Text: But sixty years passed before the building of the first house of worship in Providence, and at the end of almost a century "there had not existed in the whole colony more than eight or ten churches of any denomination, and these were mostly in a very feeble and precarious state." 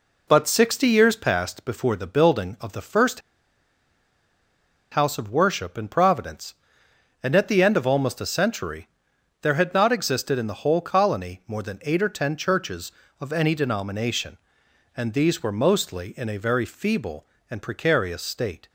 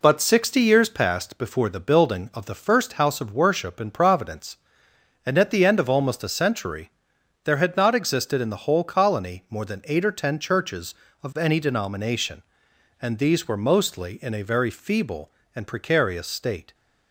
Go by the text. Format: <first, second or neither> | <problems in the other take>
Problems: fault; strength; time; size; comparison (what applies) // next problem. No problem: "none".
second | pauses between "first" and "house"; strong; at 3.2 s; 1.7 s long // pauses between "century" and "there"; noticeable; at 8.8 s; 0.54 s long; noticeable in the second